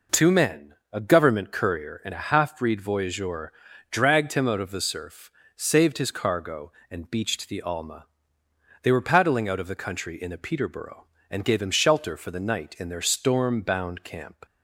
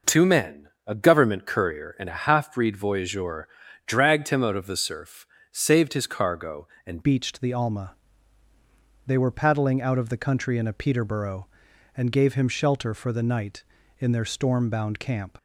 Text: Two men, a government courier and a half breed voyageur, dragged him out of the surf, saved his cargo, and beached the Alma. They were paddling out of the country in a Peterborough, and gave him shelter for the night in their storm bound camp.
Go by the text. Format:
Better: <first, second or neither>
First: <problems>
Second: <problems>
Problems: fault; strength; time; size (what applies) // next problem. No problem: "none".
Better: first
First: none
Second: changes voice at "beached"; from 7.0 s on; 8.3 s long